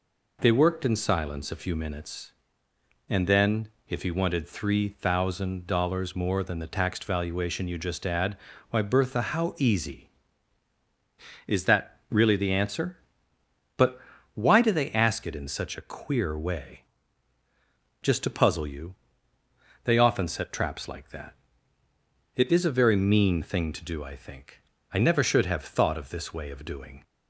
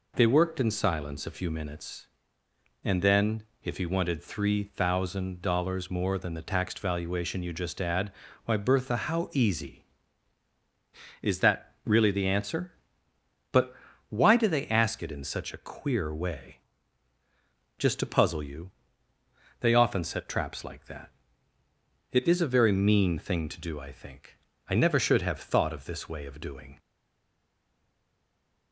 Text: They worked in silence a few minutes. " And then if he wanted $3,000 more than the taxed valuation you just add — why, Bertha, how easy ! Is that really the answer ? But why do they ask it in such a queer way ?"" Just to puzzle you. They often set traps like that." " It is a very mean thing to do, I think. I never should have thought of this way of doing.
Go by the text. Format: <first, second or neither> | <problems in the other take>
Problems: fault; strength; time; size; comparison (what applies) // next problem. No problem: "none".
first | pauses between "then" and "if"; slight; at 3.4 s; 0.22 s long; slight in the first // pauses between "But" and "why"; slight; at 13.7 s; 0.34 s long; slight in the first // stays silent after the last word; noticeable; from 26.7 s on; 2.0 s long